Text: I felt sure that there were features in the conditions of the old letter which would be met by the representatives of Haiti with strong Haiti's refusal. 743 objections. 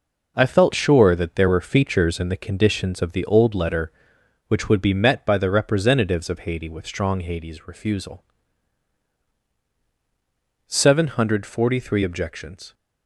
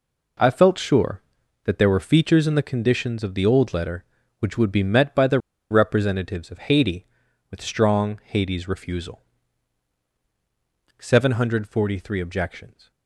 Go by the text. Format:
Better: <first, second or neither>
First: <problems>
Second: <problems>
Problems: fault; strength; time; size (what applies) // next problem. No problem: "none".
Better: first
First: none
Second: pauses between "the" and "representatives"; slight; at 5.4 s; 0.30 s long